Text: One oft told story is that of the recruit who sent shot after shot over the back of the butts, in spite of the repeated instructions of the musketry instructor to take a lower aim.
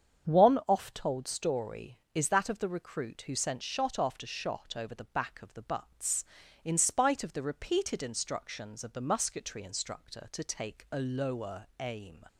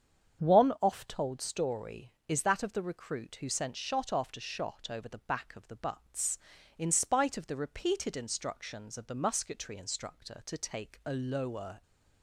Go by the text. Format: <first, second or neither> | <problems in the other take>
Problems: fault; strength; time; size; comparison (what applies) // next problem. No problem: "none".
first | starts louder than the rest; strong; until 1.4 s; 8 dB; strong in the first // stops before "aim"; at 11.8 s